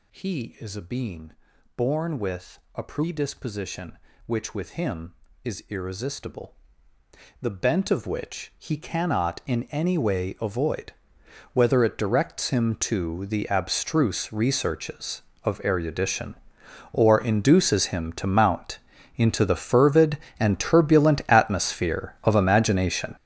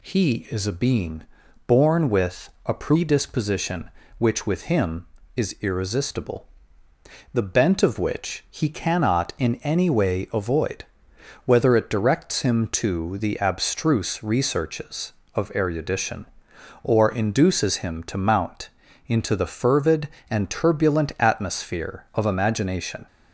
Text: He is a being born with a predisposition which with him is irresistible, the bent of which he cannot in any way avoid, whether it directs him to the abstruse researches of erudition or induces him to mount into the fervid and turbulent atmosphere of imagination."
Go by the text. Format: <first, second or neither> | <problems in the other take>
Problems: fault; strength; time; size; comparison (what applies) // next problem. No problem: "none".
second | gets louder; strong; throughout; 13.5 dB // pauses between "being" and "born"; at 1.3 s; 0.44 s long; also in the second // pauses between "with" and "a"; slight; at 2.5 s; 0.16 s long; slight in the second // pauses between "mount" and "into"; slight; at 18.7 s; 0.36 s long; slight in the second